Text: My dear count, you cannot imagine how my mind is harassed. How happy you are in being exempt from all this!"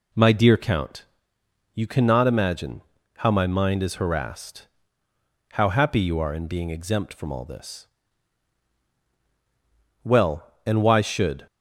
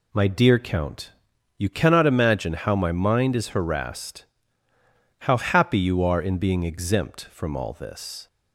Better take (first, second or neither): second